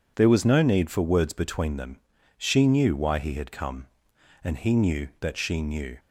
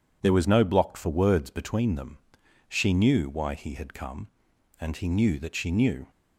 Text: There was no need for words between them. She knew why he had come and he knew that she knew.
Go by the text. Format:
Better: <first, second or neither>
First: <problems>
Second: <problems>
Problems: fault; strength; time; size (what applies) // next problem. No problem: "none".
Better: first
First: none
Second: says "block" for "need"; at 0.6 s